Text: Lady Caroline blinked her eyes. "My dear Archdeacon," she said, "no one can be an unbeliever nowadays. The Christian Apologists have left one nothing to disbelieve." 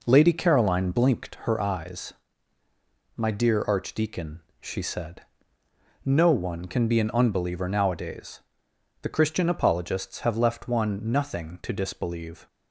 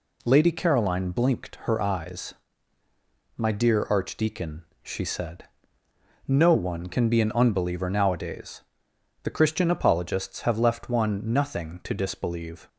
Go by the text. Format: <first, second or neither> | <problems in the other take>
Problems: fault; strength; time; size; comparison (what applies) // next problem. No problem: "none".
second | starts louder than the rest; noticeable; until 1.6 s; 4.5 dB